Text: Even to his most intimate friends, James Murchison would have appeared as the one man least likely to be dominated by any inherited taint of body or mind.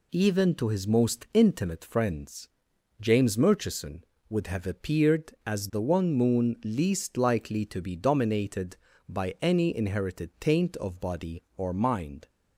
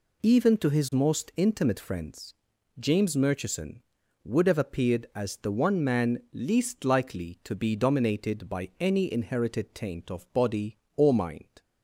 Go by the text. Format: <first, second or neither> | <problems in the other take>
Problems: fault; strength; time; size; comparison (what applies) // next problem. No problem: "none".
second | says "moon" for "man"; at 6.1 s